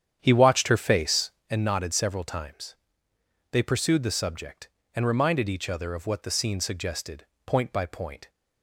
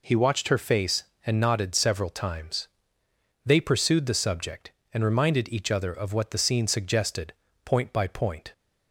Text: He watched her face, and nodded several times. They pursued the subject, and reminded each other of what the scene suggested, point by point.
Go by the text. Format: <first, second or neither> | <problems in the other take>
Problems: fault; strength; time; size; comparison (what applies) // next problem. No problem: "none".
second | starts louder than the rest; strong; until 1.5 s; 9 dB